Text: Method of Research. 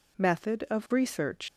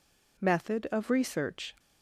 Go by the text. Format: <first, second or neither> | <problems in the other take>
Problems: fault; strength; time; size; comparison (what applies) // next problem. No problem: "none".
second | leaves "Research" unfinished; at 1.4 s; 125 ms